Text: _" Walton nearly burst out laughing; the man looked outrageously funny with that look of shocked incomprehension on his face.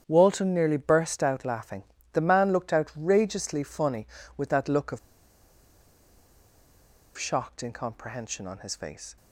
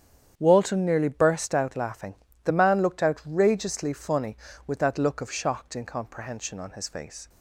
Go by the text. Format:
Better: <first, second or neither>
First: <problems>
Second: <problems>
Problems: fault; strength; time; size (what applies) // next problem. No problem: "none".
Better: second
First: starts louder than the rest; strong; until 1.0 s; 8.5 dB // pauses between "of" and "shocked"; strong; at 4.9 s; 2.1 s long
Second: starts louder than the rest; strong; until 1.3 s; 8.5 dB